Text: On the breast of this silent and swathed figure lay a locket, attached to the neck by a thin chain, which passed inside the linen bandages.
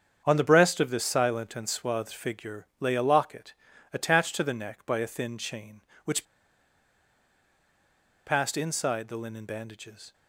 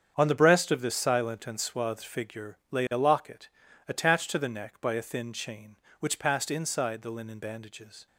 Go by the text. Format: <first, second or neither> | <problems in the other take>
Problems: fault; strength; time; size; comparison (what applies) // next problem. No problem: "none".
second | starts louder than the rest; strong; until 1.2 s; 7.5 dB; strong in the second // pauses between "which" and "passed"; strong; at 6.2 s; 2.0 s long